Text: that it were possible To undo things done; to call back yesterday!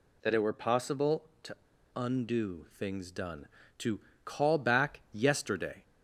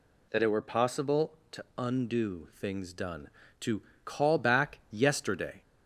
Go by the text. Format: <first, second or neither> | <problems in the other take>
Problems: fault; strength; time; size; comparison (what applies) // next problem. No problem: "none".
second | pauses between "To" and "undo"; at 1.5 s; 0.40 s long // pauses between "to" and "call"; slight; at 3.9 s; 0.26 s long; slight in the second